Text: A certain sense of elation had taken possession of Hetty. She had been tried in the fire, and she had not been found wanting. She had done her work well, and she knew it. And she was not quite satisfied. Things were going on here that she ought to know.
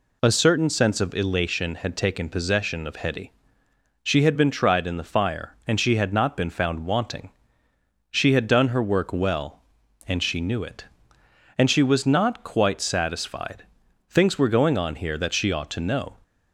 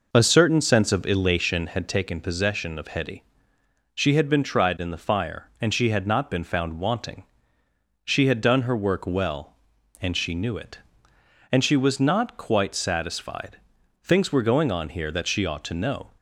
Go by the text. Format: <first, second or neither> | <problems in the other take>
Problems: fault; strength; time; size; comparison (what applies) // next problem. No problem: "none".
first | starts louder than the rest; noticeable; until 2.0 s; 5 dB